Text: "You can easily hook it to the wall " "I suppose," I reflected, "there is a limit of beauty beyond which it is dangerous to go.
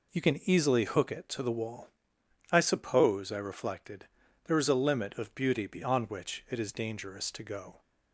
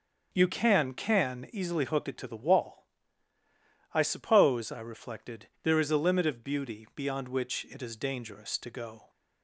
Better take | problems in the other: first | says "can" twice; at 0.9 s

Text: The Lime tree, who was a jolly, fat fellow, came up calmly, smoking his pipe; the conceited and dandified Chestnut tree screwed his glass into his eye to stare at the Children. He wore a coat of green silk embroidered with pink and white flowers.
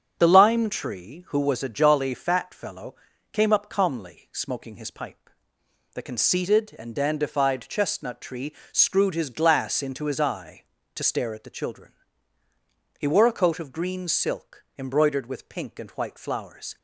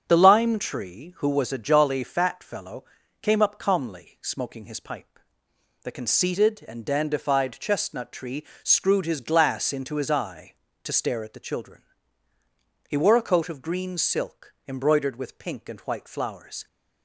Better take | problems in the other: neither | starts louder than the rest; strong; the same in both // pauses between "tree" and "screwed"; slight; the same in both // pauses between "silk" and "embroidered"; slight; the same in both

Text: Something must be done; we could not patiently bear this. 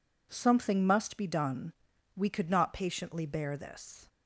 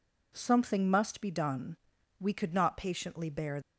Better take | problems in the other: first | stops before "this"; at 3.6 s

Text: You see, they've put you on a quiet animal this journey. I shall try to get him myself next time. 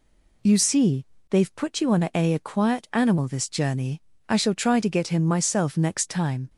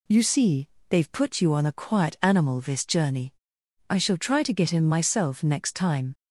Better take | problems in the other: second | says "a" twice; at 2.3 s

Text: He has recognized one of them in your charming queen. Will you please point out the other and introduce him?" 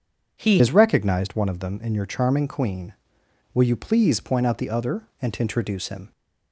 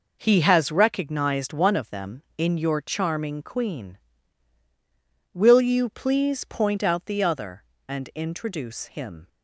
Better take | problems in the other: second | changes voice at "has"; from 0.5 s on; 5.6 s long

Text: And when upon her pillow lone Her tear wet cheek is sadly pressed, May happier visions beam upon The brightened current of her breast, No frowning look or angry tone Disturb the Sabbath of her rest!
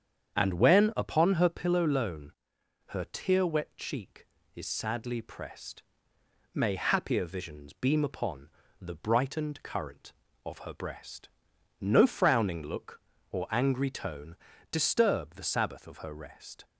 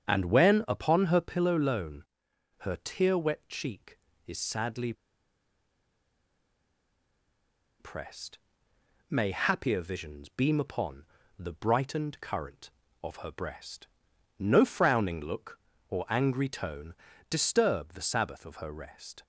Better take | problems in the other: first | starts louder than the rest; strong; until 1.0 s; 8 dB; strong in the first // pauses between "lone" and "Her"; noticeable; at 2.0 s; 0.56 s long; noticeable in the first // pauses between "sadly" and "pressed"; strong; at 4.9 s; 2.8 s long // pauses between "upon" and "The"; slight; at 11.0 s; 0.32 s long; slight in the first // pauses between "tone" and "Disturb"; slight; at 16.9 s; 0.34 s long; slight in the first

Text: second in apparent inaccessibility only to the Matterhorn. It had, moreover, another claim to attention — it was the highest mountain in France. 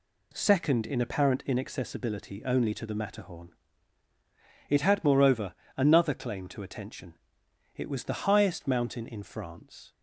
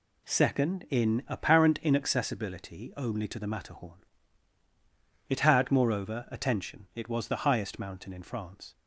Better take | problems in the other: first | skips "another claim to"; at 6.2 s

